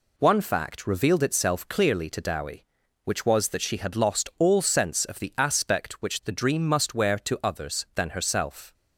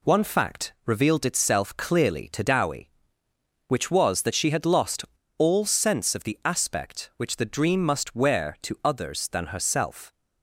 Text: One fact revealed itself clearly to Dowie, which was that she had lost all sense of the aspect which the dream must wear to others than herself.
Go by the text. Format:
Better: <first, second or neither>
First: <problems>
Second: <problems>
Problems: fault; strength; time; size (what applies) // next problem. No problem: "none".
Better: first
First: none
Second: pauses between "lost" and "all"; slight; at 5.0 s; 0.32 s long